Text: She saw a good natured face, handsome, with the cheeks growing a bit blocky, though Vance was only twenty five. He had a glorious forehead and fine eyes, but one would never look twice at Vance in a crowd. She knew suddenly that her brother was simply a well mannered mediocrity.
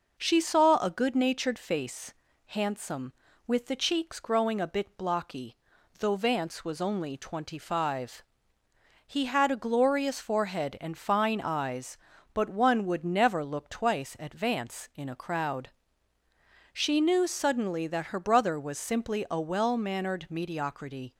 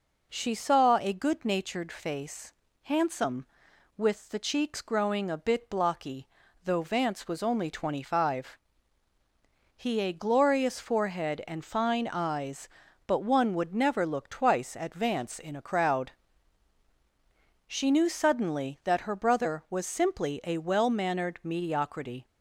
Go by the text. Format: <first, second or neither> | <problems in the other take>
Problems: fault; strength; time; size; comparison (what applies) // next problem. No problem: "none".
first | skips "had"; at 9.9 s